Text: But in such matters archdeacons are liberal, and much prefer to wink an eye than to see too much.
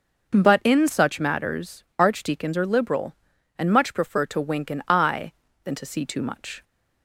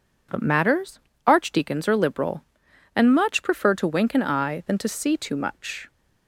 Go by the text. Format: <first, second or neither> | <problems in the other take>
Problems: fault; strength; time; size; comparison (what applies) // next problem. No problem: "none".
first | skips "in such"; at 0.4 s // pauses between "matters" and "archdeacons"; slight; at 0.9 s; 0.26 s long; slight in the first